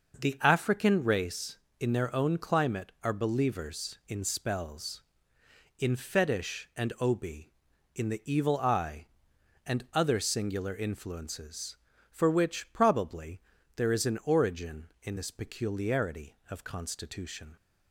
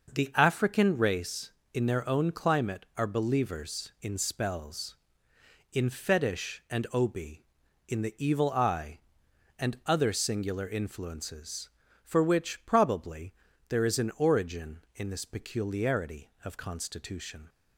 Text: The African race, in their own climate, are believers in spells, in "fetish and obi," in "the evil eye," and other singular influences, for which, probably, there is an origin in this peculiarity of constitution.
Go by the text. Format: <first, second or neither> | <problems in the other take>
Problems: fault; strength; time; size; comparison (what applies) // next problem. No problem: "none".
neither | starts louder than the rest; noticeable; the same in both